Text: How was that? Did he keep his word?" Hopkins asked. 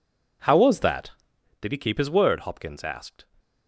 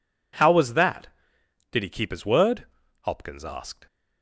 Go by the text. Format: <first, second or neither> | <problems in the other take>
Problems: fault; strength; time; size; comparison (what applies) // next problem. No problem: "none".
neither | none